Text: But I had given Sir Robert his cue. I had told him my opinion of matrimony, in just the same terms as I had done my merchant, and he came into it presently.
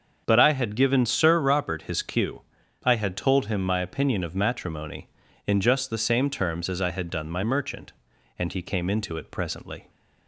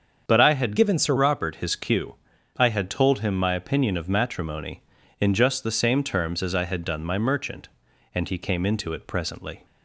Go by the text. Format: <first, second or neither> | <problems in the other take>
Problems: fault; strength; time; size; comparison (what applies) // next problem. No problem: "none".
first | starts louder than the rest; until 1.2 s; 7 dB; also in the first // changes voice from "given" to "Sir"; from 0.7 to 1.1 s; 0.4 s long